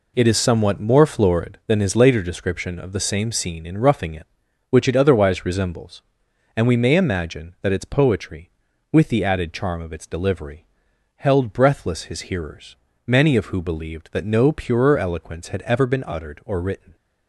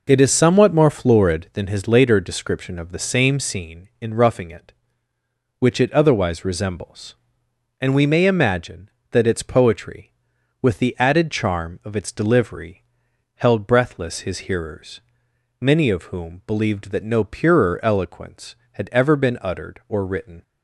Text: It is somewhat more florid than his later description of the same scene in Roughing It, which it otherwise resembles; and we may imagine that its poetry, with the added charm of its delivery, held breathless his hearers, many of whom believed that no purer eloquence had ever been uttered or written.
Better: second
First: says "who" for "whom"; at 13.4 s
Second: none

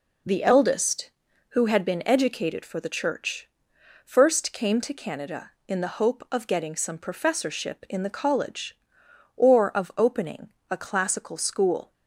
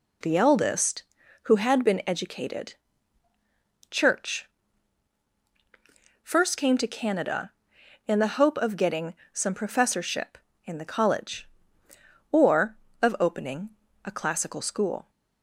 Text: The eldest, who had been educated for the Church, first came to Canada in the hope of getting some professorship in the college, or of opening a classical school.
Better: first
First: pauses between "opening" and "a"; slight; at 10.5 s; 0.20 s long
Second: skips "for the"; at 3.3 s // pauses between "getting" and "some"; slight; at 9.1 s; 0.18 s long // pauses between "opening" and "a"; slight; at 13.6 s; 0.34 s long

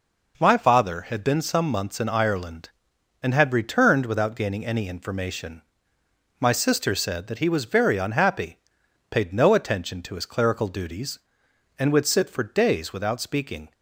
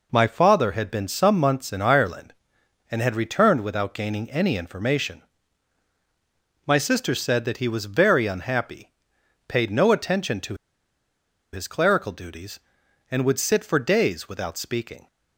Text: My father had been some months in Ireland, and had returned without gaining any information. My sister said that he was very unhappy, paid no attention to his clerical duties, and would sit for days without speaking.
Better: first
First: none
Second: pauses between "to" and "his"; at 10.5 s; 0.98 s long

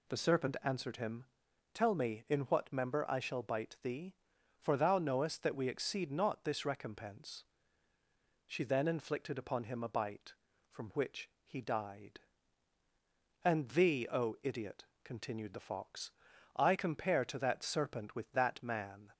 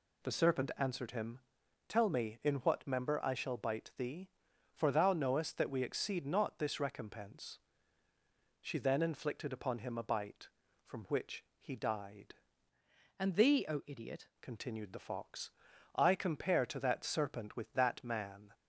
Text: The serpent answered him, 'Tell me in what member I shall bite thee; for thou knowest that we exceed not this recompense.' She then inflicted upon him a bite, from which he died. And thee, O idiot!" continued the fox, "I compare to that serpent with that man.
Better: first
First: none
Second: changes voice from "And" to "idiot"; from 13.1 to 14.2 s; 1.1 s long

